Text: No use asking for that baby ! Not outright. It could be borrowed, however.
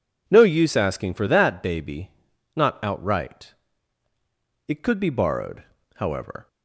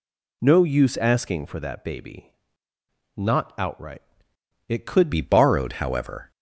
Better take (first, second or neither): first